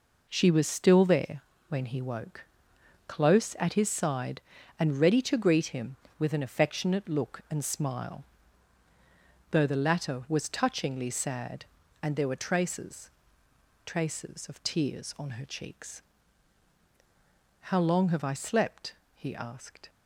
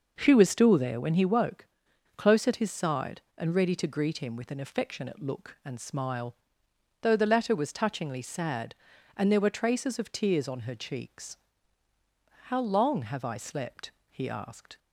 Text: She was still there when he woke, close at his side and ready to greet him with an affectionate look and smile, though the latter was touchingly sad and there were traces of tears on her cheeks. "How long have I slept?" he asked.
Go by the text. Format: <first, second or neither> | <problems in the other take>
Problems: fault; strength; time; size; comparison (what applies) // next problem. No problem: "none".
second | pauses between "there" and "when"; slight; at 1.4 s; 0.26 s long // says "traces" twice; at 13.8 s